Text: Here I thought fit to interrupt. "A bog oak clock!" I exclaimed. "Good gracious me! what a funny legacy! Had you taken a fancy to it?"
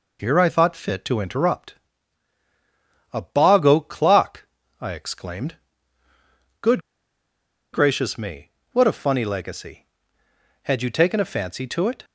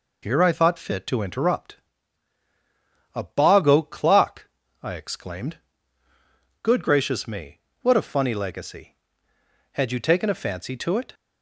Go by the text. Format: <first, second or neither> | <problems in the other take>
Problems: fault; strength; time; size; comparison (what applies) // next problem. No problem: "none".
second | pauses between "Good" and "gracious"; noticeable; at 6.8 s; 0.93 s long